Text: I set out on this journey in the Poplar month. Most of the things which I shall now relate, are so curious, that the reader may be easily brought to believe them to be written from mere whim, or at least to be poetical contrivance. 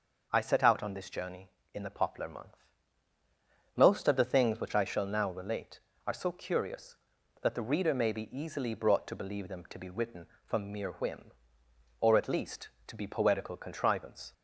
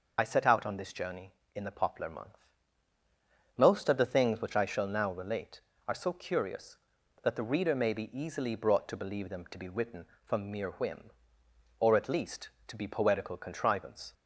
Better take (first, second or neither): first